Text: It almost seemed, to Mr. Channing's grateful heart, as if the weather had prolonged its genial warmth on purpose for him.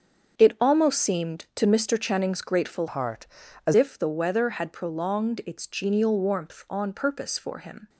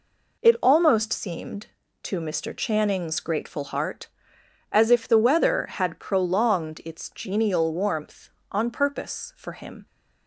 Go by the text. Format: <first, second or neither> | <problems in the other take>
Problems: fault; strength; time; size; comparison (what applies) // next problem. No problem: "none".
second | starts louder than the rest; until 1.4 s; 7 dB // changes voice from "heart" to "as"; from 2.8 to 3.7 s; 0.9 s long